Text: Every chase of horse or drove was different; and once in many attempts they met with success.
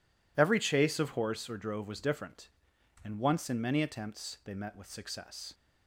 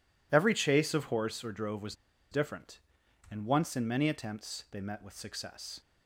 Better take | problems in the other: first | pauses between "was" and "different"; at 1.9 s; 0.36 s long

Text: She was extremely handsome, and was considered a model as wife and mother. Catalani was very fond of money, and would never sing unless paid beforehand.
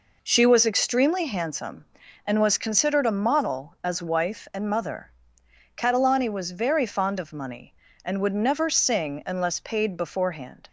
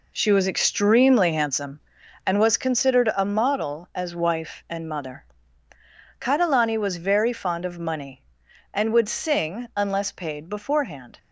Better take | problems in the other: first | skips "never"; at 9.0 s

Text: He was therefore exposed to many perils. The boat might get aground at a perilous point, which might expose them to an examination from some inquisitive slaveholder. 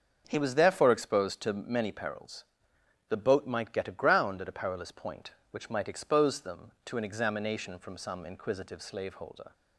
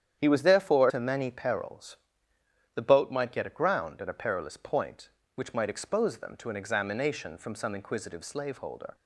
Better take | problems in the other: first | starts louder than the rest; strong; until 1.2 s; 9 dB; also in the first // skips "exposed"; at 0.8 s

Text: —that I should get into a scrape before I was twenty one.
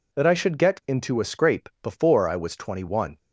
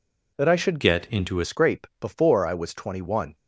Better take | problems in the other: first | changes voice from "get" to "a"; from 0.8 to 1.4 s; 0.6 s long

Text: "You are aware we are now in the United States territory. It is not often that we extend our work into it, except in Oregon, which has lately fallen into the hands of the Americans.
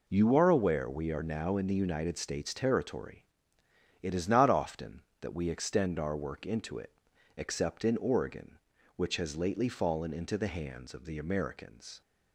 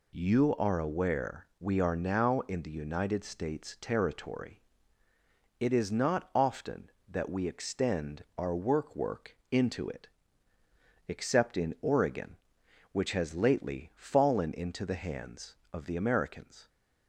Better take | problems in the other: first | says "work" twice; at 8.9 s

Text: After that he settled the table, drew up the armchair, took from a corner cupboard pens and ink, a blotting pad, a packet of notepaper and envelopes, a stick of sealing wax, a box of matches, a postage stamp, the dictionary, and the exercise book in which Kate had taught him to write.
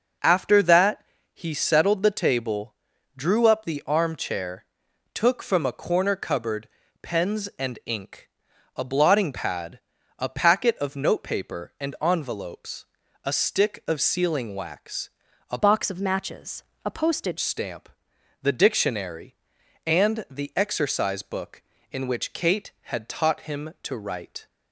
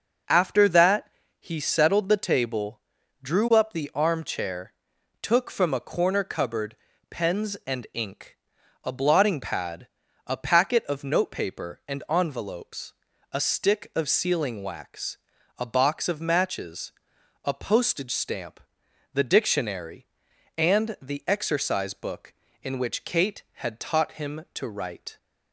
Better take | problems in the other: second | pauses between "that" and "he"; slight; at 1.0 s; 0.30 s long; slight in the second // pauses between "cupboard" and "pens"; slight; at 6.6 s; 0.36 s long; slight in the second // changes voice from "box" to "postage"; from 15.5 to 17.3 s; 1.8 s long

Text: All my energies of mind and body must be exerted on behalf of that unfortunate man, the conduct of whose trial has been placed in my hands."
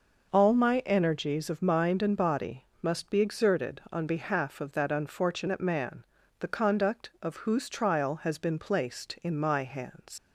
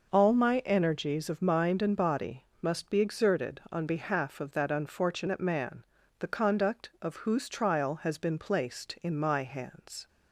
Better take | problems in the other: second | pauses between "body" and "must"; slight; at 2.6 s; 0.16 s long; slight in the second // leaves "hands" unfinished; at 10.1 s; 105 ms

